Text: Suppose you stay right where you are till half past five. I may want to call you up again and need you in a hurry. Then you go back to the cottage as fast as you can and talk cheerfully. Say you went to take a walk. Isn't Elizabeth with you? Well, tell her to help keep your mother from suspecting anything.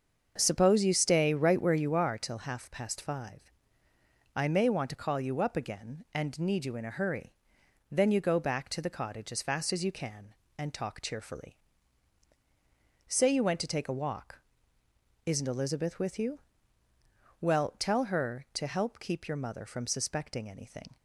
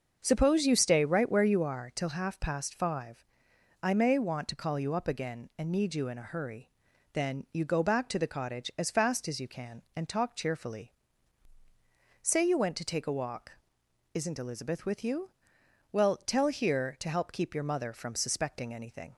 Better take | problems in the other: first | starts louder than the rest; until 1.2 s; 6.5 dB; also in the first // says "here" for "her"; at 16.4 s

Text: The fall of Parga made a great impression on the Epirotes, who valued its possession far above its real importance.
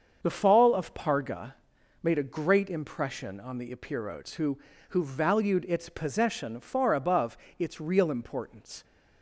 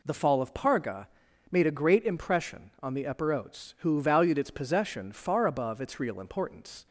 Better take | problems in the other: second | starts louder than the rest; until 1.2 s; 7 dB // pauses between "Parga" and "made"; noticeable; at 1.5 s; 0.48 s long; also in the second // says "who" twice; at 4.8 s // pauses between "above" and "its"; slight; at 7.3 s; 0.20 s long

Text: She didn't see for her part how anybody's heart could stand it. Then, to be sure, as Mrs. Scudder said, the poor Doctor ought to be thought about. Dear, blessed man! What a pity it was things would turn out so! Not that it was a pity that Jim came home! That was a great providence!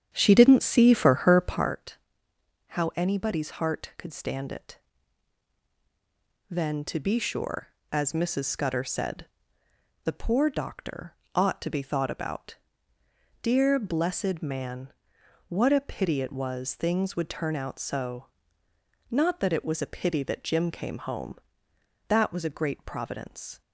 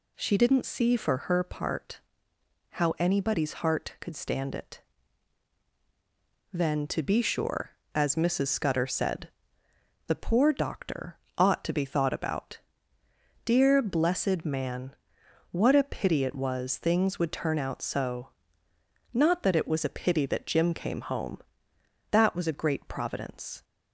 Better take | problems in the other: second | starts louder than the rest; strong; until 1.7 s; 9.5 dB // pauses between "part" and "how"; noticeable; at 1.9 s; 0.72 s long; noticeable in the second // pauses between "Doctor" and "ought"; slight; at 11.1 s; 0.20 s long; slight in the second

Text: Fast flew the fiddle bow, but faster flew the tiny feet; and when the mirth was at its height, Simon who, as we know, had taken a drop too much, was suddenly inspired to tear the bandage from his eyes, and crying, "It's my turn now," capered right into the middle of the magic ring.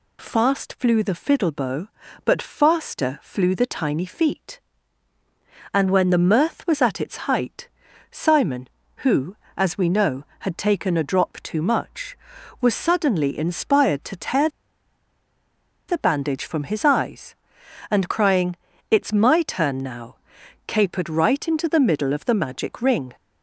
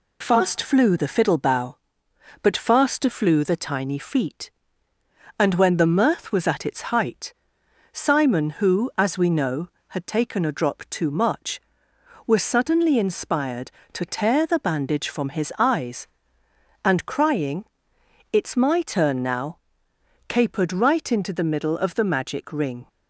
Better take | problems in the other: second | pauses between "tear" and "the"; strong; at 14.4 s; 1.3 s long

